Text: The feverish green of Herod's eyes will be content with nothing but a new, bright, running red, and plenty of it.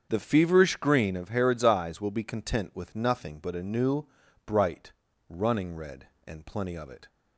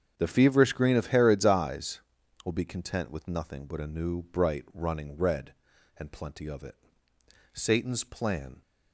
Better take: first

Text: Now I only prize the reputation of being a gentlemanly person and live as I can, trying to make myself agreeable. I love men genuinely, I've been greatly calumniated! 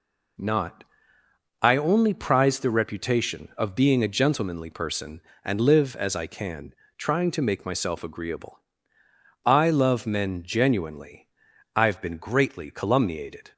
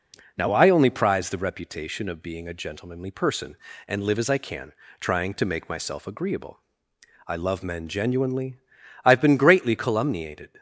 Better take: second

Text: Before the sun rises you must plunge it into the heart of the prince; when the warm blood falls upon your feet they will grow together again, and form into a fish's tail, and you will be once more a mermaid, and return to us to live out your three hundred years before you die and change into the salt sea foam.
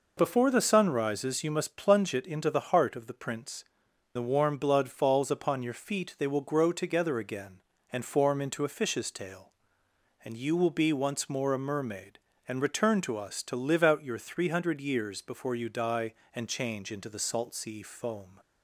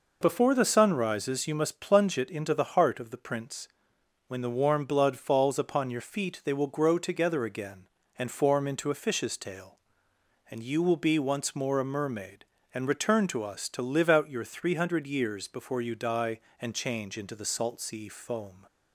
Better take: second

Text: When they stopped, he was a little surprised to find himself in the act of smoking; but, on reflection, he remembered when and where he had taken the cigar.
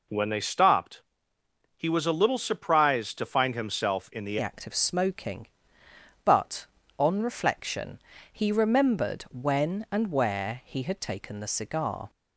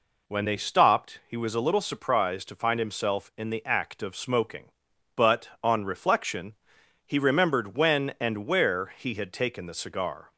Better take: second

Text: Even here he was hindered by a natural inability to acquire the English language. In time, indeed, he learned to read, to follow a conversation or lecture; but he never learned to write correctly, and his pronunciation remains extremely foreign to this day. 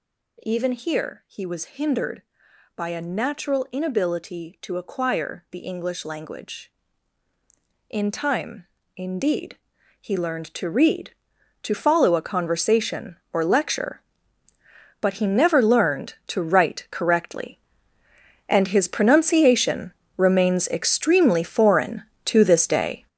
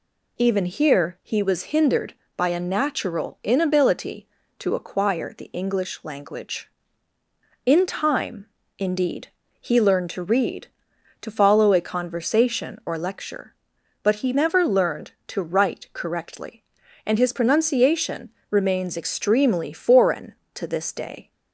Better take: second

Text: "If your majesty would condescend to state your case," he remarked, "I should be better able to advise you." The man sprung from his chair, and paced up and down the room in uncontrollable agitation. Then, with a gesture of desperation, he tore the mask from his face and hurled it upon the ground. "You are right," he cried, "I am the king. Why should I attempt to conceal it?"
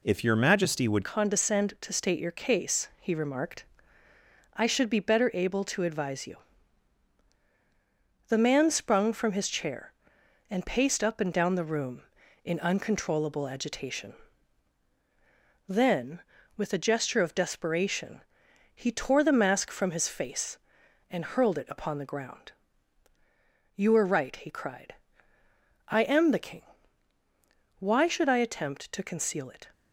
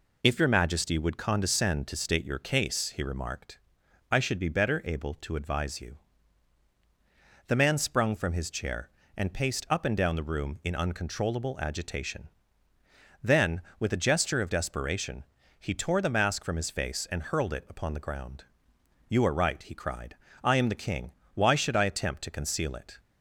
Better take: second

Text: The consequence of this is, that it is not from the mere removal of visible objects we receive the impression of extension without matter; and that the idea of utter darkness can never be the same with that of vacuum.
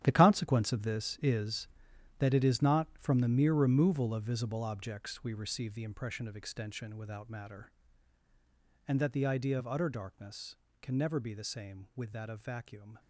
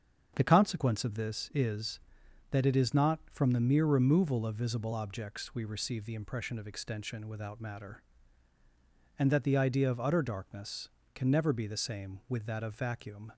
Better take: second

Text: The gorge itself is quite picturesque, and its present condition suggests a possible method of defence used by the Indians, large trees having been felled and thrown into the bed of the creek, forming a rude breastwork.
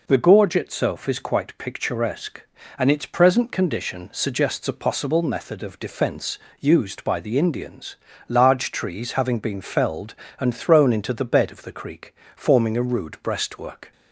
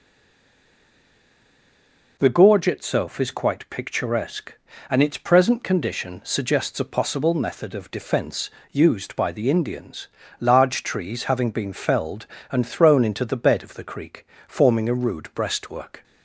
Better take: first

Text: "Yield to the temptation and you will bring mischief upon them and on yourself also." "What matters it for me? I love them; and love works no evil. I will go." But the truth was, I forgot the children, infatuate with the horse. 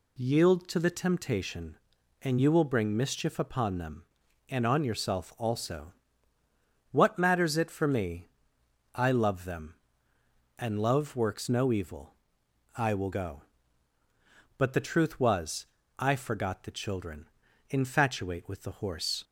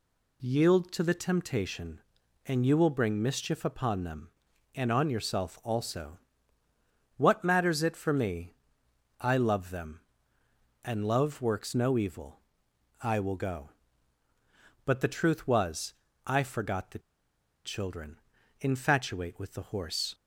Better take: first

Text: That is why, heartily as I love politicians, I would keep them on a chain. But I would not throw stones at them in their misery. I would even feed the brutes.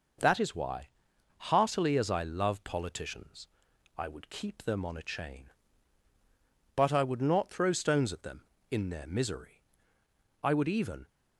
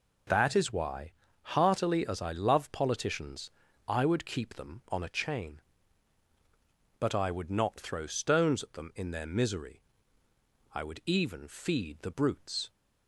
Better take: second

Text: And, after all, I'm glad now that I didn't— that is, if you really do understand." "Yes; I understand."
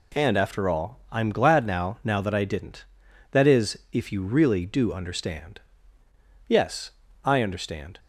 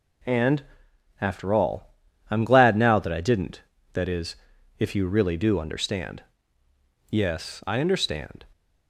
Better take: second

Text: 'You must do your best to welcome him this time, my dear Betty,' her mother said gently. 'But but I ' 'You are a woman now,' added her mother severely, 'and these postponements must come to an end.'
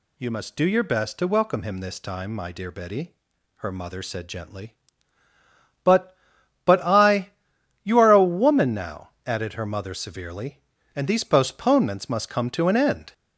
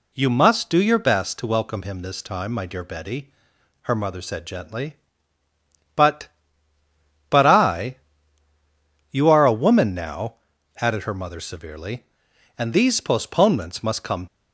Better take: first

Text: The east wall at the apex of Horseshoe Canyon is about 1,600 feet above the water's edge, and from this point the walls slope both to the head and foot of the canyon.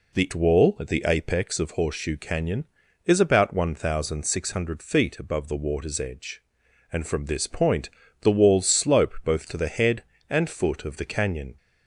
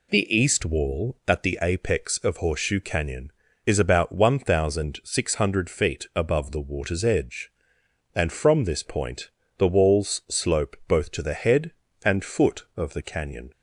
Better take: second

